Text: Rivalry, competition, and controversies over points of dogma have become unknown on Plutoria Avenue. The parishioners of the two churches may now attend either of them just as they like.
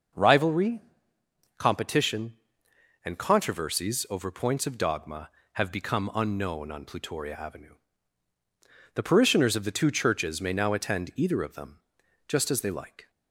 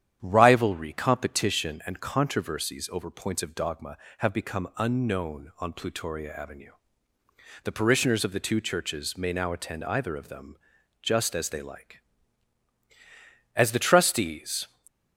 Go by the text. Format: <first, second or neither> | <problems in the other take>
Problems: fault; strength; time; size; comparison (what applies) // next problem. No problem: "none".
first | starts louder than the rest; strong; until 1.2 s; 9.5 dB // pauses between "them" and "just"; at 10.5 s; 0.44 s long; noticeable in the first // goes on to say "As the trustees"; noticeable; from 13.5 s on; 1.1 s long